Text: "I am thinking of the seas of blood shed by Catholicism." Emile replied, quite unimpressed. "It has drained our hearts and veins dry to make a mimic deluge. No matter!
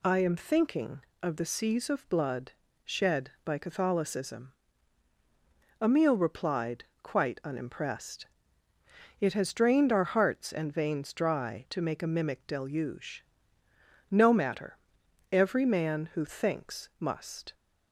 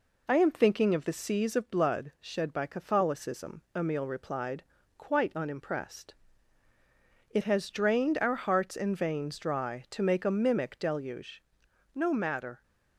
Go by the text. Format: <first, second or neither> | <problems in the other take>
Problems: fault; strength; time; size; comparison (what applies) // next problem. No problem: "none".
second | pauses between "blood" and "shed"; slight; at 2.5 s; 0.30 s long // goes on to say "Every man who thinks must"; strong; from 15.3 s on; 2.2 s long